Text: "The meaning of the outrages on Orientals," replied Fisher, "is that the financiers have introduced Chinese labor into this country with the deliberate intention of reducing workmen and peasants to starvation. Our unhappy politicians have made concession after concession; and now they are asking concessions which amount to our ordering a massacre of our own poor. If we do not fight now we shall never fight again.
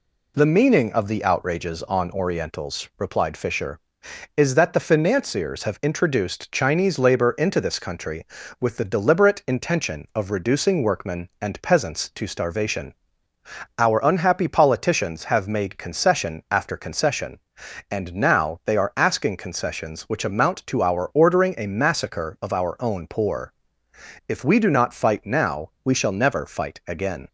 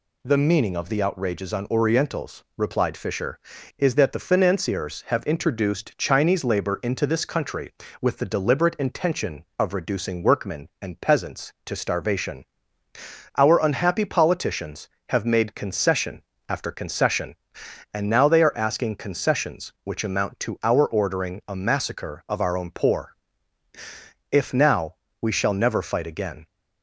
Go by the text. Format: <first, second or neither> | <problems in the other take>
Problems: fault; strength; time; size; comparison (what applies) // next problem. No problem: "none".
first | pauses between "concession" and "after"; slight; at 16.2 s; 0.30 s long // skips "we do not fight"; at 24.5 s // pauses between "now" and "we"; slight; at 24.9 s; 0.26 s long